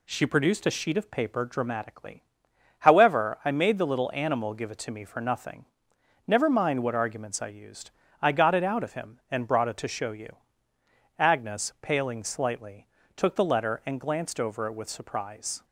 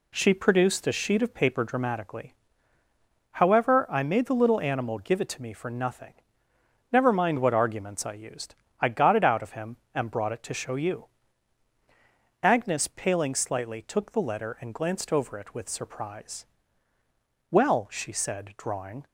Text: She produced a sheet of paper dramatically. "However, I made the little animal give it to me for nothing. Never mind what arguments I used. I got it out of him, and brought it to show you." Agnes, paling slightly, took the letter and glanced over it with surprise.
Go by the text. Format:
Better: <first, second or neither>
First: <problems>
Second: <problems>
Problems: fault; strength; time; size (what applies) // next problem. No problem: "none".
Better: first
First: none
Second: goes on to say "Well she said drawing"; from 17.4 s on; 1.5 s long